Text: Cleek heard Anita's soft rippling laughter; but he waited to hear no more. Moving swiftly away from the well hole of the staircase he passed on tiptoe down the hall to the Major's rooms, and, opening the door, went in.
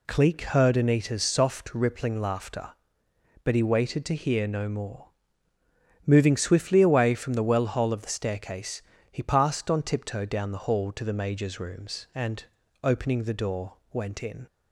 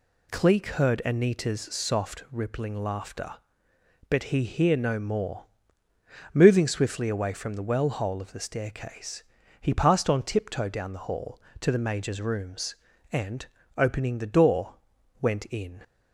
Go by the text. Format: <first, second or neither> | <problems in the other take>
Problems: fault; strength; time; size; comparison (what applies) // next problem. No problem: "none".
first | skips "waited to"; at 4.4 s // pauses between "staircase" and "he"; slight; at 9.2 s; 0.36 s long; slight in the first